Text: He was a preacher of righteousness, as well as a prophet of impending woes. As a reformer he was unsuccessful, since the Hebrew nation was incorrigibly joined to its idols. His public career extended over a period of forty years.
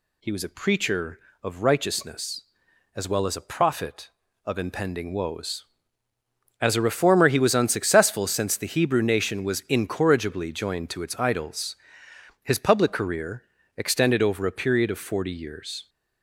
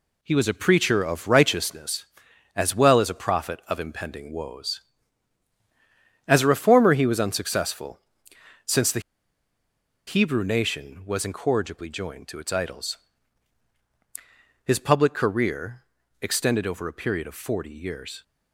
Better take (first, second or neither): first